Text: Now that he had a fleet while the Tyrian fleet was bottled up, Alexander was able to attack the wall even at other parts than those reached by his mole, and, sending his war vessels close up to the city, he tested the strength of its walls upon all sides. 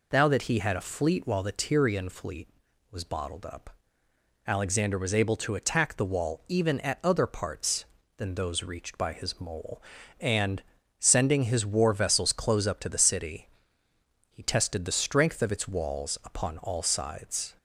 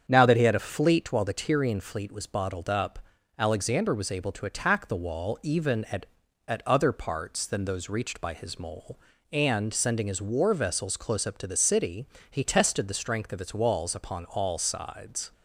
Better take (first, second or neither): first